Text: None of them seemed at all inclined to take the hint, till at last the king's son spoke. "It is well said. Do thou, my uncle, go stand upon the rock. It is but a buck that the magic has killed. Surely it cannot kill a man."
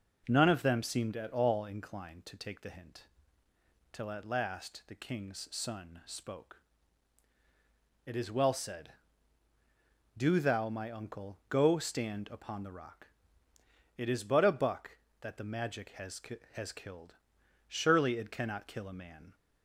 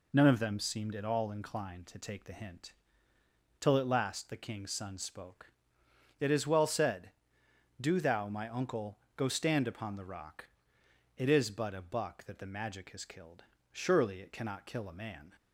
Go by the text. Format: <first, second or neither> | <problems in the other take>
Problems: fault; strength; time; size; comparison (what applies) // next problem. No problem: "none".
second | says "has" twice; at 16.5 s